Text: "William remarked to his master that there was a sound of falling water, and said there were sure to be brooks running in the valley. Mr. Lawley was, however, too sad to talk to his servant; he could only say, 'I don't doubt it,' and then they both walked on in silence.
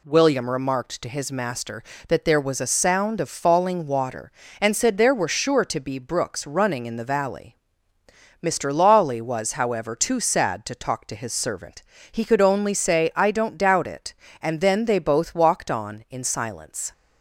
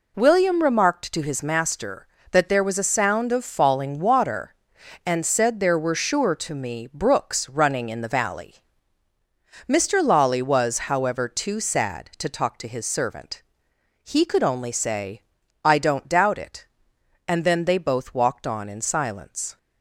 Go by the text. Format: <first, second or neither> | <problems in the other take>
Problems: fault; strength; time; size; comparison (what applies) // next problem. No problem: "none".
first | says "me" for "be"; at 6.5 s